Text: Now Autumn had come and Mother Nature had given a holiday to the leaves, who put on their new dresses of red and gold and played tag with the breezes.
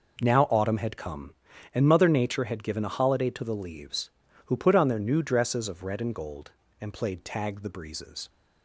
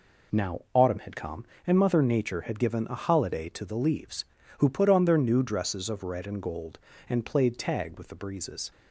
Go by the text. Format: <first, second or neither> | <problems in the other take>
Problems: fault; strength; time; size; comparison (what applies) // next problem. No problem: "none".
second | skips "with"; at 7.6 s